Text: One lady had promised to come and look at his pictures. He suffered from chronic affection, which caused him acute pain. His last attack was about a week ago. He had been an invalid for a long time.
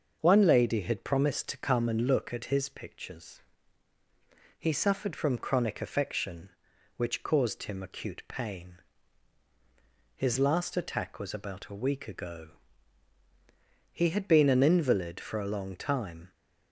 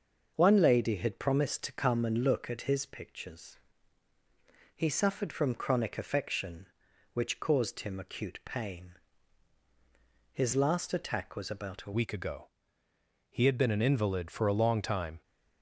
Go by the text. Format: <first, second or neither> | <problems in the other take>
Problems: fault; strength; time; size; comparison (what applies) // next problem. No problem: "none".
first | starts louder than the rest; until 1.3 s; 6.5 dB; also in the first // changes voice at "week"; from 11.9 s on; 3.3 s long